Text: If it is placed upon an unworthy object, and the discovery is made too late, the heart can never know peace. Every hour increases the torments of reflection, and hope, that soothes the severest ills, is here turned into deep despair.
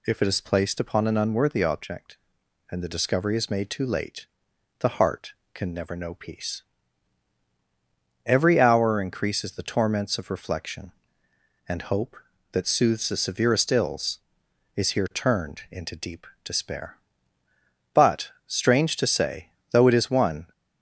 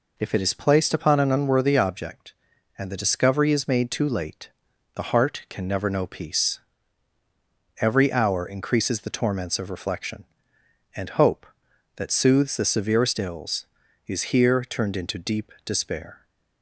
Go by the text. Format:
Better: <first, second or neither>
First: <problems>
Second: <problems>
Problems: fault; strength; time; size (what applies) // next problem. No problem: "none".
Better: second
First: pauses between "deep" and "despair"; slight; at 16.2 s; 0.18 s long // goes on to say "But strange to say though it is one"; strong; from 17.9 s on; 2.5 s long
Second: none